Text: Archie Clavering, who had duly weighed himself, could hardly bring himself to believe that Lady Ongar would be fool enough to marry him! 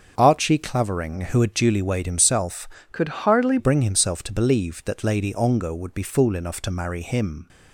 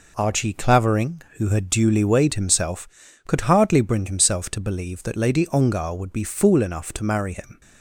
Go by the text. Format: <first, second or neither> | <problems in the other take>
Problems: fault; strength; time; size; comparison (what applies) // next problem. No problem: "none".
second | starts louder than the rest; until 1.1 s; 7 dB // changes voice from "could" to "hardly"; from 2.9 to 3.5 s; 0.6 s long